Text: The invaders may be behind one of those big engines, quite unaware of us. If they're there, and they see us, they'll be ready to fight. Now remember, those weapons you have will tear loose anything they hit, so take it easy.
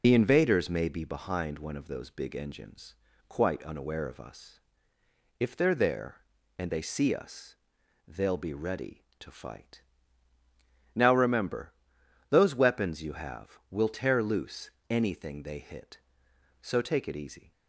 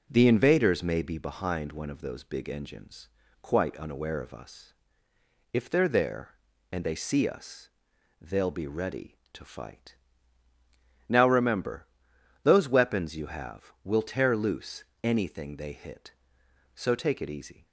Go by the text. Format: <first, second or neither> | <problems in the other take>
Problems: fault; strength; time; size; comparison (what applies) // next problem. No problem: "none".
second | loses the start of "The"; at 0.0 s; 80 ms // pauses between "loose" and "anything"; slight; at 14.6 s; 0.20 s long; slight in the second